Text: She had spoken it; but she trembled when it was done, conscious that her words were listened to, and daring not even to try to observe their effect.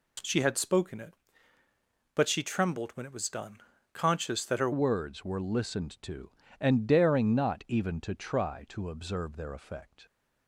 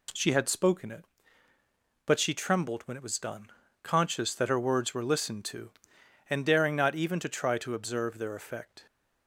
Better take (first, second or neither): second